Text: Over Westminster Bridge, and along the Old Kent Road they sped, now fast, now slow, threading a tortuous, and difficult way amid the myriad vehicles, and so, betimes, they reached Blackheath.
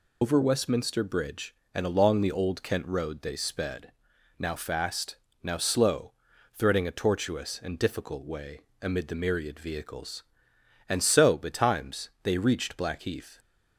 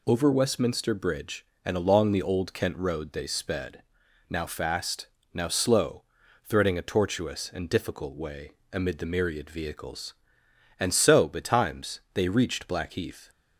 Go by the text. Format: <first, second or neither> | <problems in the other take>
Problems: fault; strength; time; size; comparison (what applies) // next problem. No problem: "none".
second | loses the start of "Over"; at 0.2 s; 65 ms // pauses between "way" and "amid"; slight; at 8.6 s; 0.20 s long; slight in the second